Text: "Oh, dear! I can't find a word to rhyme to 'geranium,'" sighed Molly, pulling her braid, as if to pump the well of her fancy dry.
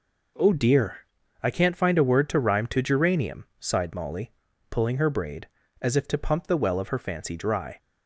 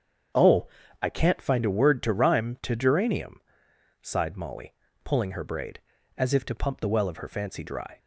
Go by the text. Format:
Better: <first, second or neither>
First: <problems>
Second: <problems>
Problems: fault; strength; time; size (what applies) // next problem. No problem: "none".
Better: first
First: none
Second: starts louder than the rest; strong; until 1.6 s; 7.5 dB // skips "dear"; at 0.8 s